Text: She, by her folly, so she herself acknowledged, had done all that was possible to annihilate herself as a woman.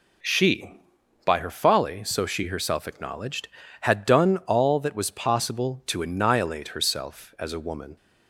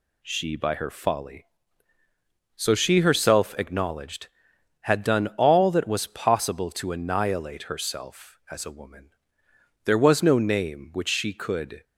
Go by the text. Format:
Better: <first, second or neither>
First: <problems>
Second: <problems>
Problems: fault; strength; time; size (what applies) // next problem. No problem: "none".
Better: first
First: none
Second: goes on to say "There was no name which she could"; strong; from 9.8 s on; 2.0 s long